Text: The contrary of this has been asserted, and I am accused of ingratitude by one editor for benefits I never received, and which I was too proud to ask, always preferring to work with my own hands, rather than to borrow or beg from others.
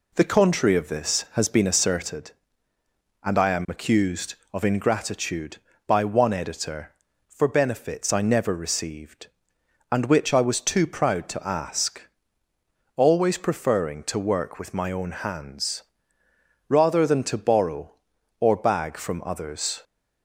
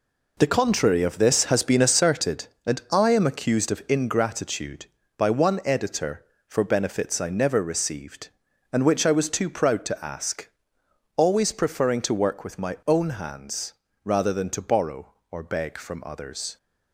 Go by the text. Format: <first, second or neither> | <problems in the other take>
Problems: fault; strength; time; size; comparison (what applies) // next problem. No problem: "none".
second | says "bag" for "beg"; at 18.5 s